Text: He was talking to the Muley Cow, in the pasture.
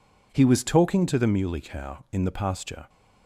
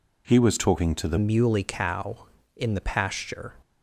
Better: first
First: none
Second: changes voice at "Muley"; from 1.1 s on; 2.4 s long

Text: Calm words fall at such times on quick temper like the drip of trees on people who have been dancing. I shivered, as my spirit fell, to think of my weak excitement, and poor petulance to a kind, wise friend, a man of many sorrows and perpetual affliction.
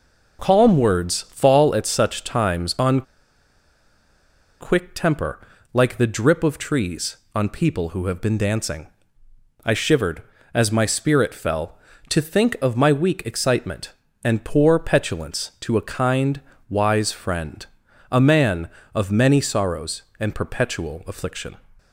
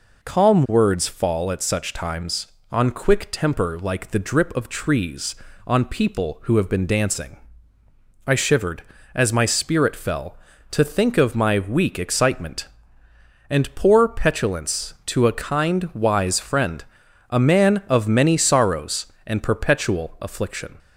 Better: second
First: pauses between "on" and "quick"; strong; at 3.0 s; 1.5 s long // pauses between "temper" and "like"; slight; at 5.3 s; 0.32 s long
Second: none

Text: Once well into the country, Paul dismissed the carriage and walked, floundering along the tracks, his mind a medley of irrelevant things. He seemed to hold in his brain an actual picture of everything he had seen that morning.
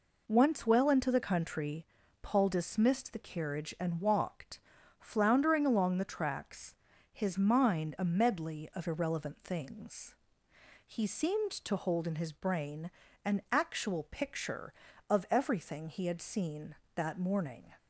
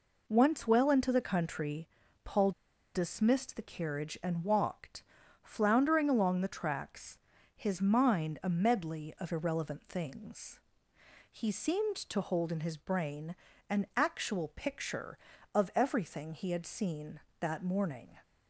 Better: first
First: pauses between "brain" and "an"; slight; at 12.8 s; 0.36 s long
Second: pauses between "Paul" and "dismissed"; at 2.5 s; 0.44 s long // pauses between "brain" and "an"; slight; at 13.3 s; 0.36 s long

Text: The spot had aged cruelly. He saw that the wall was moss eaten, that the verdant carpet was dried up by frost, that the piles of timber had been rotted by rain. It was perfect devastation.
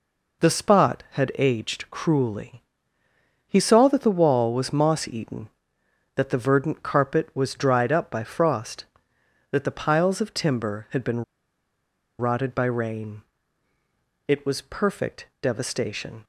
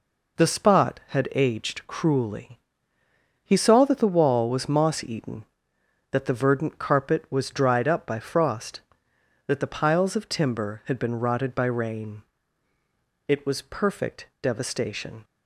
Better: second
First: pauses between "been" and "rotted"; noticeable; at 11.2 s; 0.95 s long // pauses between "perfect" and "devastation"; slight; at 15.2 s; 0.16 s long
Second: pauses between "perfect" and "devastation"; slight; at 14.2 s; 0.16 s long

